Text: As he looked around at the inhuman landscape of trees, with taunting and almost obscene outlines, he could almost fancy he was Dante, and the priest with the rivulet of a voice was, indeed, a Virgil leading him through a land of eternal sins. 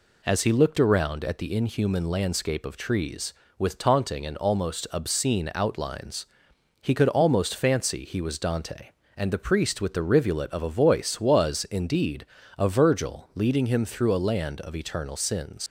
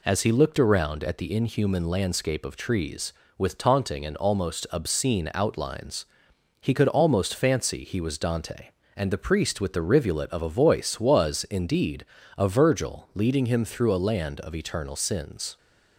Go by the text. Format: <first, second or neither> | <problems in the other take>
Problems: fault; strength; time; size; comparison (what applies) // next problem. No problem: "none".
second | leaves "sins" unfinished; at 15.6 s; 110 ms